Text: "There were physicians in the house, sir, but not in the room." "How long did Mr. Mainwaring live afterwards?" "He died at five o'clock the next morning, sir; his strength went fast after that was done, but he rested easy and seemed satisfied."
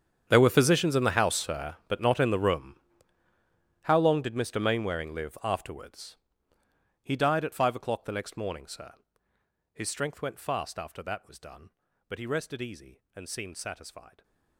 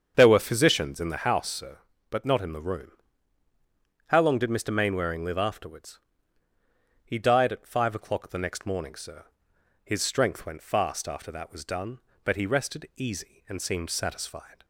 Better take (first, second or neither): second